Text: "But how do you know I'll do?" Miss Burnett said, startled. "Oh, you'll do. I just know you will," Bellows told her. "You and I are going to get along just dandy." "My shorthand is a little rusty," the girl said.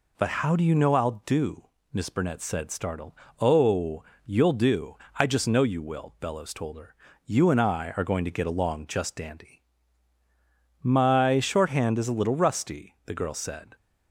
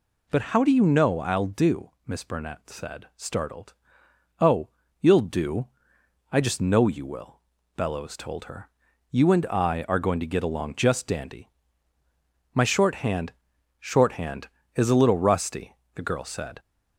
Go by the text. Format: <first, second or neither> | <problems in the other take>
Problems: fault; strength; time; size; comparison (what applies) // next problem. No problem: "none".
first | says "shorthand" twice; at 13.7 s